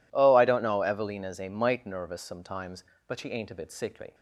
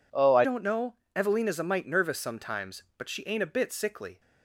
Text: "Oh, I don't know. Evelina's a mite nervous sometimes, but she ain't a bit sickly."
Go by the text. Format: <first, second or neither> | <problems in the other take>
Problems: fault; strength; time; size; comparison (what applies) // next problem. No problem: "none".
first | changes voice at "don't"; from 0.4 s on; 3.7 s long